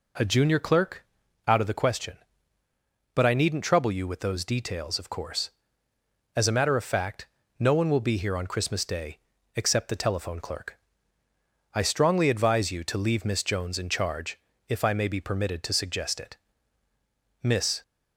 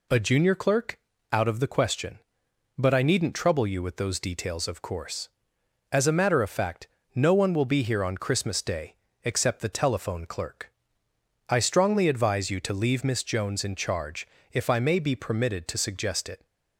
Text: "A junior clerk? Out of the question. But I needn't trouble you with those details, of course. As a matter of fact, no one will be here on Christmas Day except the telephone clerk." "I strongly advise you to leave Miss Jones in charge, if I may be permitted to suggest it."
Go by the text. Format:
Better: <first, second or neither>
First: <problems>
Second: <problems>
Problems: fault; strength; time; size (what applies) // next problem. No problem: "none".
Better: second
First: pauses between "Day" and "except"; at 9.1 s; 0.38 s long // goes on to say "Miss"; slight; from 17.4 s on; 0.40 s long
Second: pauses between "Day" and "except"; slight; at 8.9 s; 0.30 s long